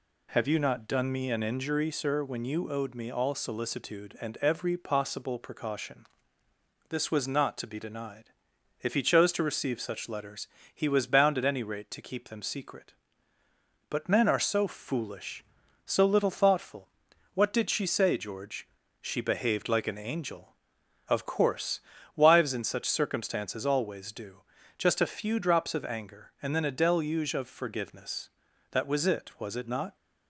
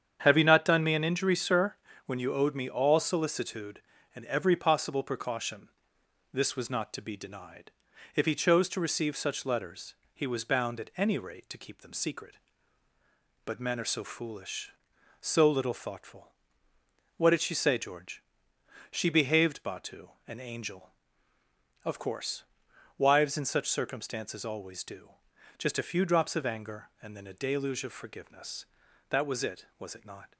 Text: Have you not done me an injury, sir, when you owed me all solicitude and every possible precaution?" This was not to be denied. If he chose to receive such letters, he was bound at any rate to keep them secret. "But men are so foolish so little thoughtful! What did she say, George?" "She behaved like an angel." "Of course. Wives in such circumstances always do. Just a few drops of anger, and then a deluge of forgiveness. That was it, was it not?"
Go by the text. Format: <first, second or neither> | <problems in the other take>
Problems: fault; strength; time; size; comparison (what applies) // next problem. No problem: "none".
first | starts louder than the rest; strong; until 1.2 s; 8.5 dB // says "batu" for "like"; at 19.6 s